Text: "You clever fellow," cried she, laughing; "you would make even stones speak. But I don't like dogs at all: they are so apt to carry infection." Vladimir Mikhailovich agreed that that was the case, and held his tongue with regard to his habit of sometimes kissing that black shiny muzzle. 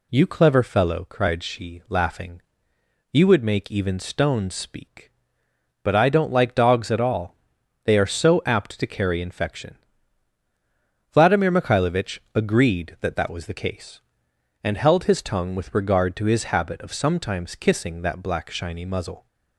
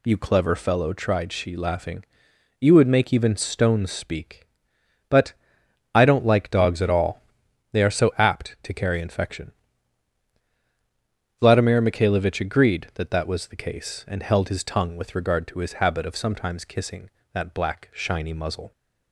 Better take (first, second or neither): first